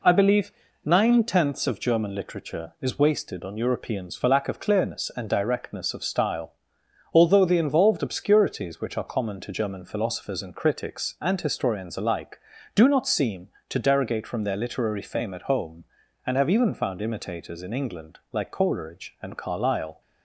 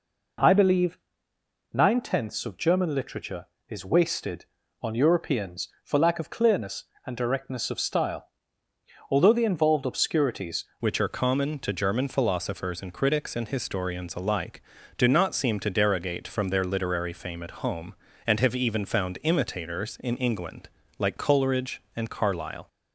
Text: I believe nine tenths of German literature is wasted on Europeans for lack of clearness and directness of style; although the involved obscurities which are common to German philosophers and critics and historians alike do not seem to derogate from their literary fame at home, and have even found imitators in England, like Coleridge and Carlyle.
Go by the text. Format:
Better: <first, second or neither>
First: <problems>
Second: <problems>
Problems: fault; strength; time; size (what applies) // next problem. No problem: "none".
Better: first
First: pauses between "believe" and "nine"; slight; at 0.5 s; 0.32 s long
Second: pauses between "believe" and "nine"; noticeable; at 0.9 s; 0.76 s long // changes voice at "which"; from 10.7 s on; 11.9 s long